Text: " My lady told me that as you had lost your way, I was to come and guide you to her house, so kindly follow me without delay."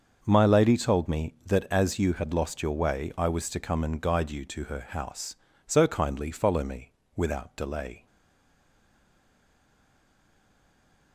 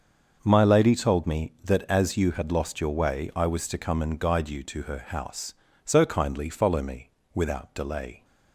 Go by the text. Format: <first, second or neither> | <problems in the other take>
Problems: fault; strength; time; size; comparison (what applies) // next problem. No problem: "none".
second | starts louder than the rest; until 1.2 s; 6.5 dB; also in the second // pauses between "me" and "without"; slight; at 6.9 s; 0.24 s long; slight in the second // stays silent after the last word; strong; from 8.0 s on; 3.1 s long